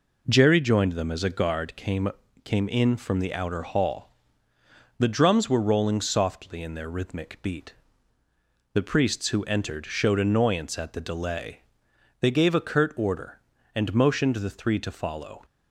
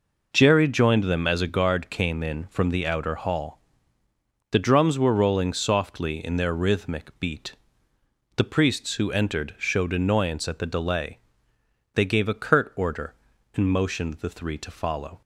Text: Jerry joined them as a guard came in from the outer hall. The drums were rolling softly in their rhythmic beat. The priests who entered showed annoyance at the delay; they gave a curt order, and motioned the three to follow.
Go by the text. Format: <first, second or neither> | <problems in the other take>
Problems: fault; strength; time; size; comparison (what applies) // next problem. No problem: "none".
second | says "came" twice; at 2.4 s